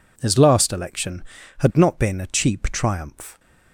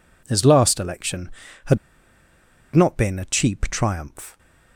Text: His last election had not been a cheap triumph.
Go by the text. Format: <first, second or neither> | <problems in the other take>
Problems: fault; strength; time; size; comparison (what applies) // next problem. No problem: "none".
first | pauses between "had" and "not"; noticeable; at 1.7 s; 0.97 s long